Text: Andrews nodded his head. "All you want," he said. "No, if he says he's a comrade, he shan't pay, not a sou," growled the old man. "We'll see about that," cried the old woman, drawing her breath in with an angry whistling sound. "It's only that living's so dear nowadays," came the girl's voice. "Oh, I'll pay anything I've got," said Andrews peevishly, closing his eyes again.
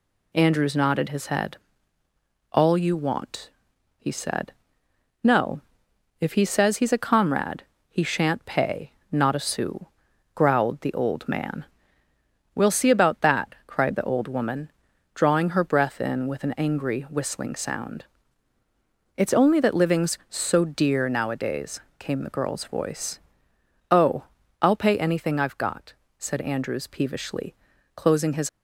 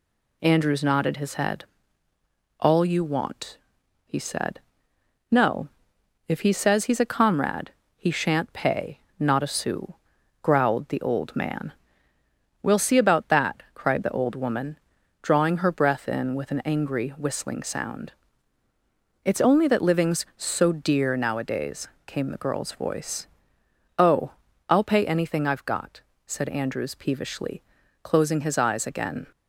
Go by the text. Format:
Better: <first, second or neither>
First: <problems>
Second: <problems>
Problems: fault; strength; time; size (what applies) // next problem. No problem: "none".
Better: second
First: stops before "eyes again"; at 28.4 s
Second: none